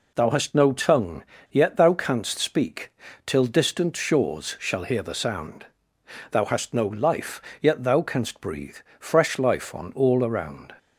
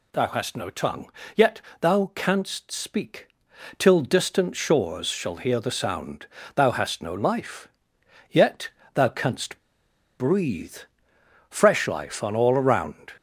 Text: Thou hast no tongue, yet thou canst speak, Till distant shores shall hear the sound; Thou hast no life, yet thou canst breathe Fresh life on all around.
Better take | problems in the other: first | pauses between "yet" and "thou"; slight; at 1.6 s; 0.20 s long // pauses between "yet" and "thou"; slight; at 8.7 s; 0.24 s long // pauses between "canst" and "breathe"; noticeable; at 9.6 s; 0.57 s long // pauses between "breathe" and "Fresh"; noticeable; at 10.7 s; 0.72 s long; slight in the first

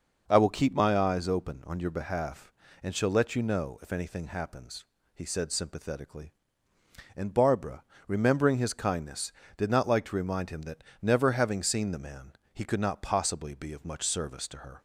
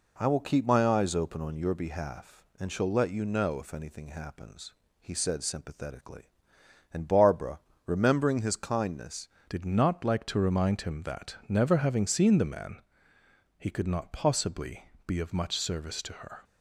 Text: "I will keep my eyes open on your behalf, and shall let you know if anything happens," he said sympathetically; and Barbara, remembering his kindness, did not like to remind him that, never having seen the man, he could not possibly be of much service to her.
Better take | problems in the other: first | changes voice at "did"; from 9.4 s on; 7.0 s long // pauses between "possibly" and "be"; slight; at 14.8 s; 0.22 s long

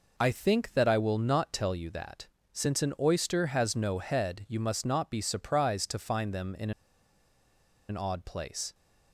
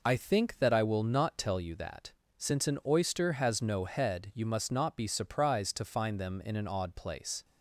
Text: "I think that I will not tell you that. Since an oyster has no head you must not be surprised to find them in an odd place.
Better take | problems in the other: second | pauses between "in" and "an"; at 6.7 s; 1.1 s long

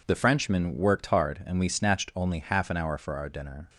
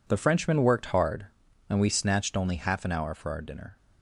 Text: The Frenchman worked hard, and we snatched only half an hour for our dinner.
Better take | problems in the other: neither | none

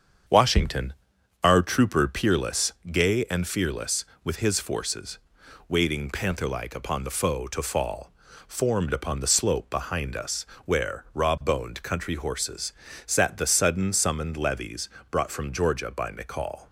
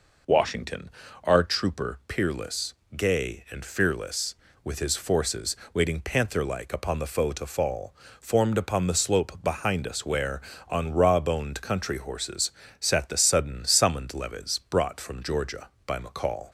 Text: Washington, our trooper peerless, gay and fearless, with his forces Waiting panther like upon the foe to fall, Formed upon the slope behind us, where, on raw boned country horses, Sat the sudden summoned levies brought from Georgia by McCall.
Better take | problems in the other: second | starts louder than the rest; strong; until 1.8 s; 7.5 dB // pauses between "forces" and "Waiting"; noticeable; at 5.1 s; 0.50 s long; slight in the second // skips "on"; at 11.0 s // pauses between "levies" and "brought"; slight; at 14.8 s; 0.22 s long

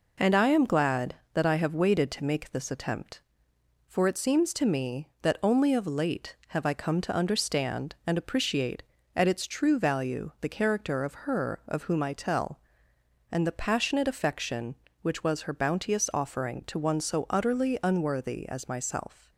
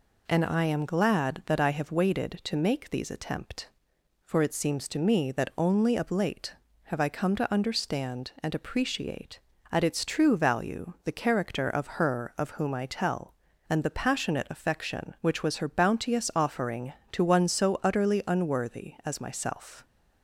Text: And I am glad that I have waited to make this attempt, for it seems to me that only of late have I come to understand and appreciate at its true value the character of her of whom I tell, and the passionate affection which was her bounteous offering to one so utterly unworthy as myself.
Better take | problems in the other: first | says "these" for "this"; at 2.8 s

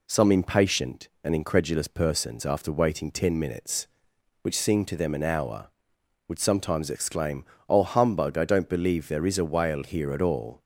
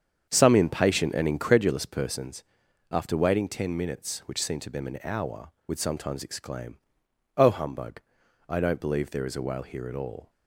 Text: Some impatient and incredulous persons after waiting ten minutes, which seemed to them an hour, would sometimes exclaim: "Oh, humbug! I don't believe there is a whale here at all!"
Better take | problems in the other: first | starts louder than the rest; strong; until 1.9 s; 7.5 dB // pauses between "persons" and "after"; noticeable; at 2.4 s; 0.48 s long

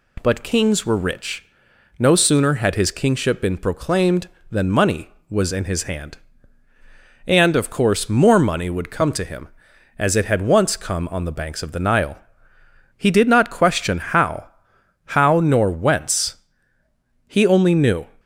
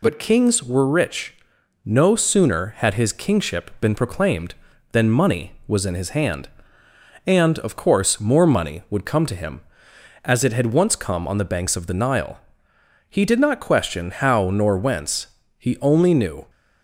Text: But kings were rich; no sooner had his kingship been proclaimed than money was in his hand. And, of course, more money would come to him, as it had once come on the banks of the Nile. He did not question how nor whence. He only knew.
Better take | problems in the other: second | says "how" twice; at 15.1 s

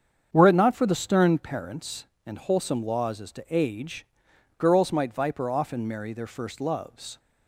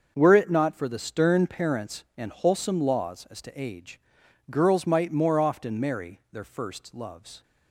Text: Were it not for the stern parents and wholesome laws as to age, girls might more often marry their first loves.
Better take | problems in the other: second | starts louder than the rest; strong; until 1.3 s; 7.5 dB; also in the second // says "viper" for "more"; at 5.1 s

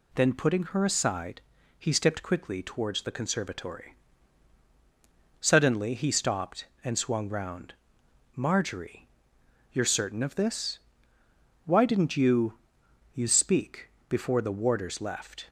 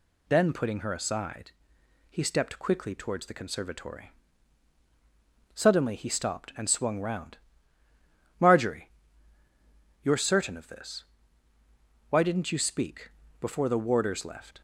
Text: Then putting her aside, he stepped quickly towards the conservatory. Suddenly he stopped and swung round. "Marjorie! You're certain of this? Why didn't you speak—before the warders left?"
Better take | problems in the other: second | says "you" twice; at 13.1 s

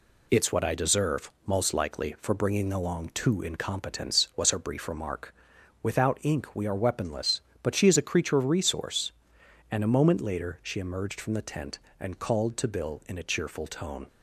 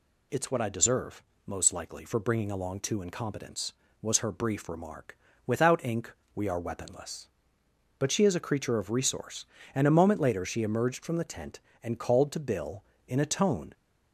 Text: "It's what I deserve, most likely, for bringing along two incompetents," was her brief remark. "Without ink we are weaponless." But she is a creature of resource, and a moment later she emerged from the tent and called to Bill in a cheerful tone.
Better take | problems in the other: first | pauses between "ink" and "we"; slight; at 6.1 s; 0.24 s long // skips "cheerful"; at 13.2 s

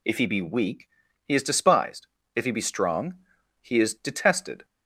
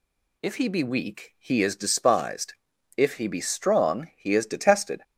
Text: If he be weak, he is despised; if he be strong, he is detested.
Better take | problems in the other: neither | none

